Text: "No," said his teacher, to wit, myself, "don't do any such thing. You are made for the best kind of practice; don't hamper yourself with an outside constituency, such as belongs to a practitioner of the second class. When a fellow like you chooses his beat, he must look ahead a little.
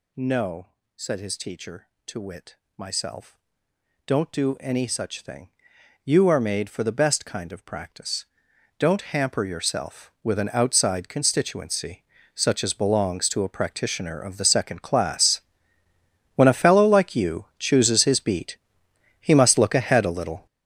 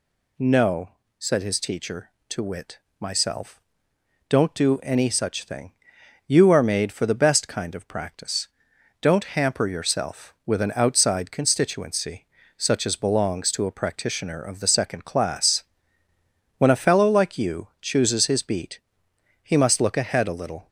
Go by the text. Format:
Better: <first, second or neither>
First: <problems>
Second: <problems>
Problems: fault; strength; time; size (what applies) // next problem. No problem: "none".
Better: second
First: gets louder; strong; throughout; 11.5 dB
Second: none